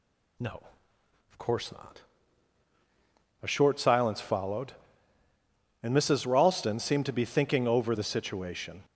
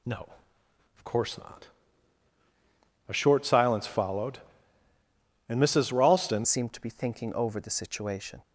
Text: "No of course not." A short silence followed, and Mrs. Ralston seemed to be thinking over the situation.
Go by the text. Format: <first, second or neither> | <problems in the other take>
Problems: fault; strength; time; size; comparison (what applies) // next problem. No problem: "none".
first | changes voice at "seemed"; from 6.4 s on; 2.0 s long